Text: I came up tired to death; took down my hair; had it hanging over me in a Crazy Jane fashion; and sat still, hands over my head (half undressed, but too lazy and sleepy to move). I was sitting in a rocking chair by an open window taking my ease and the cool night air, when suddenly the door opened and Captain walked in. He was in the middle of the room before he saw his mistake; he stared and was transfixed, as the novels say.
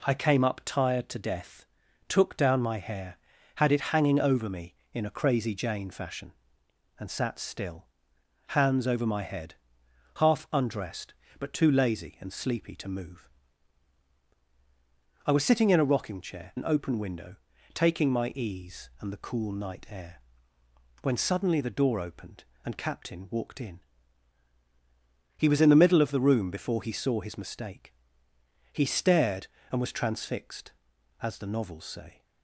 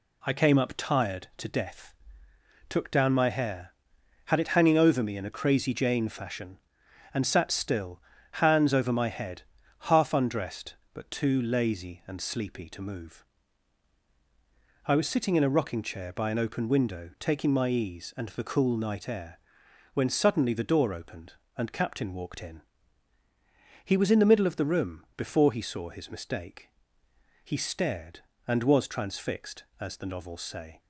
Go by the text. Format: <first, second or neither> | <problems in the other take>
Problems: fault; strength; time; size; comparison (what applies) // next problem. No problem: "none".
second | skips "by"; at 16.5 s // pauses between "window" and "taking"; slight; at 17.3 s; 0.36 s long